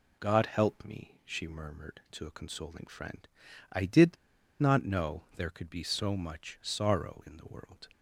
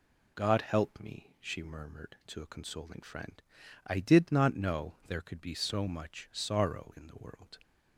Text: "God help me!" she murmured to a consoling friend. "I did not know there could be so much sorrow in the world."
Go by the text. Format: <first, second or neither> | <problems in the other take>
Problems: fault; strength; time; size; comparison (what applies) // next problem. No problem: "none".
second | pauses between "did" and "not"; at 4.1 s; 0.43 s long